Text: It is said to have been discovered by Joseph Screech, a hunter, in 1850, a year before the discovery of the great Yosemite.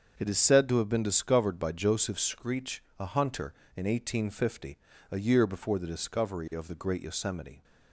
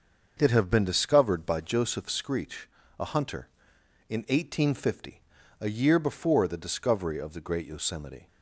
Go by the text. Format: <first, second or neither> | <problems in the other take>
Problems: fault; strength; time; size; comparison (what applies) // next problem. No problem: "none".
first | starts louder than the rest; until 1.4 s; 6.5 dB; also in the first // skips "is said to"; at 0.5 s